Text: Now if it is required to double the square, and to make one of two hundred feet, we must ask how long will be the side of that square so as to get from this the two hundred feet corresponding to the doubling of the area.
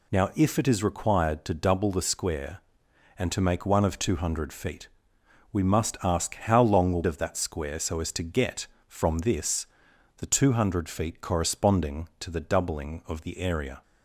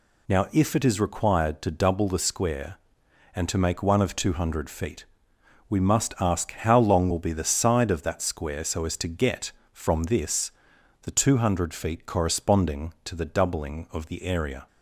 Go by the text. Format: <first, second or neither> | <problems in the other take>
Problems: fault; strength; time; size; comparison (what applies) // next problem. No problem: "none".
second | skips "be the side"; at 7.0 s // pauses between "this" and "the"; noticeable; at 9.6 s; 0.52 s long; noticeable in the second